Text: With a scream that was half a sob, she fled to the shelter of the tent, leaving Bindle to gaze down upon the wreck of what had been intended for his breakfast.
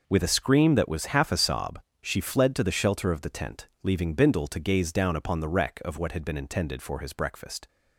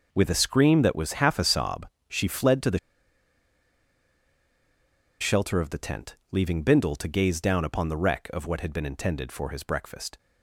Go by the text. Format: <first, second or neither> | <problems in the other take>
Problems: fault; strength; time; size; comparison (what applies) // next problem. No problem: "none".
first | pauses between "the" and "shelter"; strong; at 2.7 s; 2.4 s long